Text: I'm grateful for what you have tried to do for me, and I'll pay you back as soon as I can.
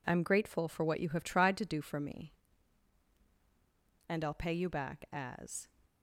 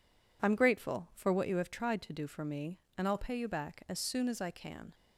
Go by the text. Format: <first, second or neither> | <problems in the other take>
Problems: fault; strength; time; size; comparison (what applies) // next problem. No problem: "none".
second | stops before "soon as I can"; at 5.8 s